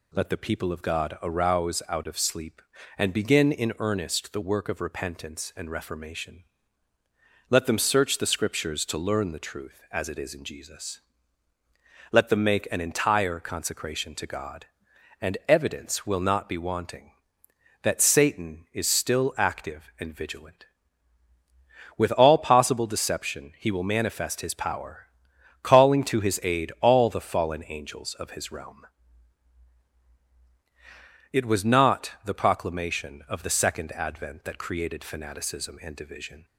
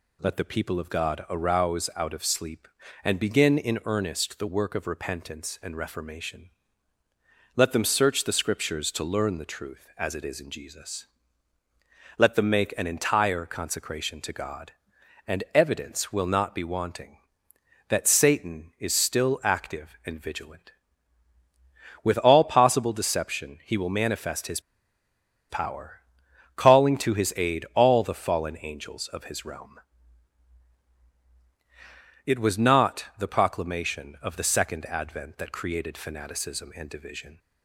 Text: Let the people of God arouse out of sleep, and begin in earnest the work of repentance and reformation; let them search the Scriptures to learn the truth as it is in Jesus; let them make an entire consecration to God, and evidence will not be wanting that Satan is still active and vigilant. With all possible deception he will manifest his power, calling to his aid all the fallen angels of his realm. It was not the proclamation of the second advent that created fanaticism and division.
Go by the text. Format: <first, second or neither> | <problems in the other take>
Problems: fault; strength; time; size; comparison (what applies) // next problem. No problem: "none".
first | pauses between "his" and "power"; noticeable; at 24.5 s; 0.90 s long